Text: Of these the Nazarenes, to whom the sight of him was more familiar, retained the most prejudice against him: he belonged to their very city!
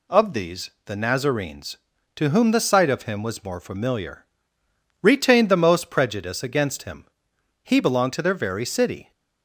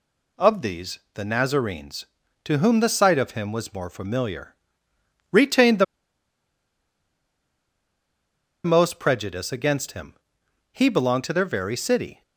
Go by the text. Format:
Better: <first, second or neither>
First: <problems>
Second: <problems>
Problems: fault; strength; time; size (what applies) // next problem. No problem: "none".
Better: first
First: pauses between "these" and "the"; slight; at 0.6 s; 0.16 s long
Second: pauses between "these" and "the"; slight; at 0.9 s; 0.16 s long // pauses between "the" and "most"; strong; at 5.8 s; 2.8 s long